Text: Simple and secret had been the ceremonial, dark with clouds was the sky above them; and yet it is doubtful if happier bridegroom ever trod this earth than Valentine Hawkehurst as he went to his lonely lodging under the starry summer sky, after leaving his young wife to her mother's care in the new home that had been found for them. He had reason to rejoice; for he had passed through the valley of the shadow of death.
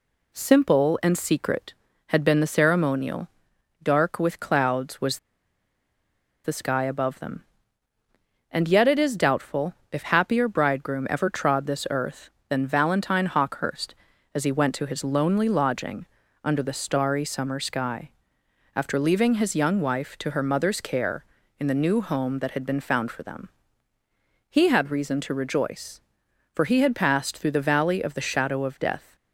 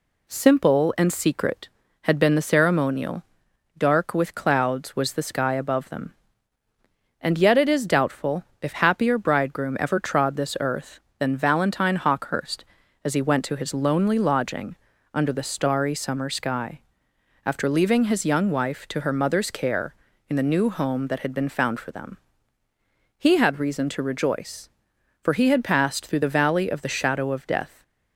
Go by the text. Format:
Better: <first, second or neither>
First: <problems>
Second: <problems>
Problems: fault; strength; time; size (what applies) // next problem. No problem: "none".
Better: second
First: pauses between "was" and "the"; strong; at 5.1 s; 1.2 s long // pauses between "doubtful" and "if"; slight; at 9.7 s; 0.18 s long // pauses between "lodging" and "under"; at 16.0 s; 0.38 s long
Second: pauses between "doubtful" and "if"; slight; at 8.4 s; 0.18 s long // pauses between "lodging" and "under"; at 14.7 s; 0.38 s long